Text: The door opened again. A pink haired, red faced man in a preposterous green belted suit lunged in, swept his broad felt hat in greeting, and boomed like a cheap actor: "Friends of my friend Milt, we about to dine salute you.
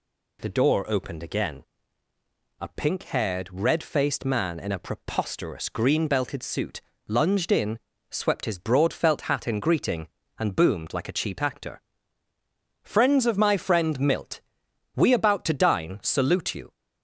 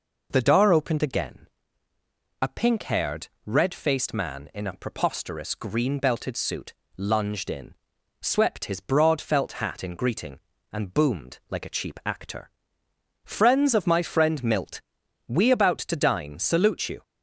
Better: neither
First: pauses between "suit" and "lunged"; slight; at 6.8 s; 0.28 s long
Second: pauses between "suit" and "lunged"; slight; at 6.7 s; 0.24 s long

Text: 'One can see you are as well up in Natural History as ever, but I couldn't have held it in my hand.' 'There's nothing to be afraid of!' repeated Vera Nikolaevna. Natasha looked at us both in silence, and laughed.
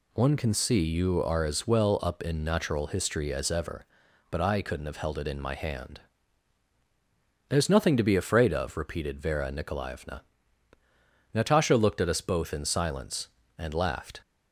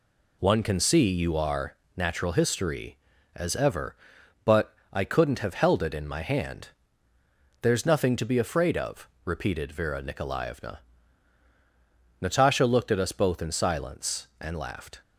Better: first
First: none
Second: skips "as well up in"; at 1.8 s // pauses between "but" and "I"; slight; at 4.7 s; 0.16 s long

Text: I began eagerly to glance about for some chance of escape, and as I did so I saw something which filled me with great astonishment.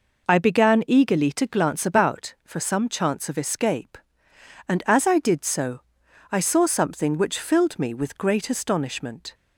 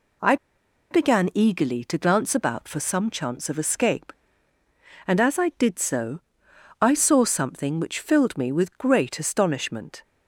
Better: first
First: pauses between "so" and "I"; noticeable; at 5.7 s; 0.50 s long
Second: pauses between "I" and "began"; noticeable; at 0.3 s; 0.55 s long // pauses between "so" and "I"; noticeable; at 6.2 s; 0.60 s long

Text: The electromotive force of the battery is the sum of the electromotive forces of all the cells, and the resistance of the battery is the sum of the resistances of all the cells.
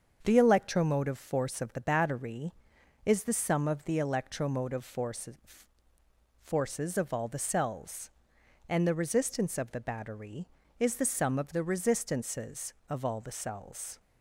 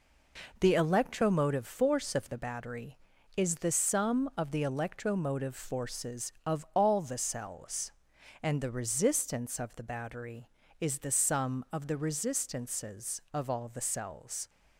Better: second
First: starts louder than the rest; until 1.2 s; 7 dB // says "forces" twice; at 6.4 s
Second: none

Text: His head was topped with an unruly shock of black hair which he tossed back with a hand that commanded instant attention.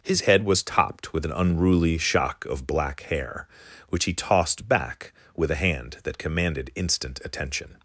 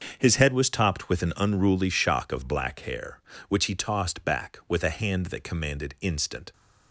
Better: first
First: none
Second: starts louder than the rest; until 1.1 s; 6.5 dB // stops before "attention"; at 6.5 s

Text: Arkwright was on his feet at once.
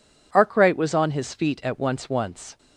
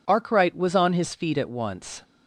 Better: second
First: says "once" twice; at 2.0 s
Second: none

